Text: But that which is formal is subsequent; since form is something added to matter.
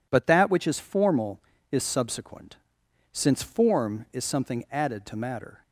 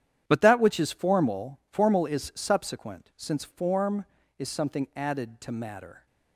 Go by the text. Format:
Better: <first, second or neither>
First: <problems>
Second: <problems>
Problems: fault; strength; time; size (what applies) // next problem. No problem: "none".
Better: first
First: none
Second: starts louder than the rest; strong; until 1.2 s; 10.5 dB // says "formal" twice; at 1.6 s